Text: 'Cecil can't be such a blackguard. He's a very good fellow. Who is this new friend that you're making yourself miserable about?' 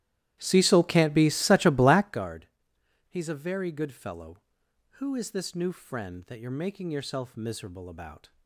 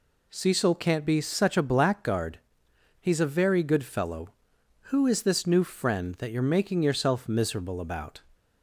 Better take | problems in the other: second | starts louder than the rest; strong; until 2.3 s; 13.5 dB

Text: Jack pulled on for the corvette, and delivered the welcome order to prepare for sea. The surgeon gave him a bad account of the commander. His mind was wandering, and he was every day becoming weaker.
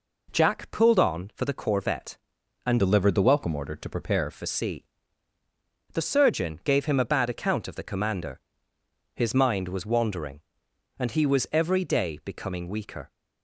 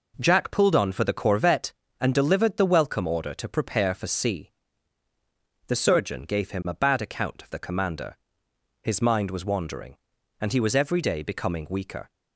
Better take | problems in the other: second | changes voice from "delivered" to "prepare"; from 2.7 to 4.3 s; 1.6 s long

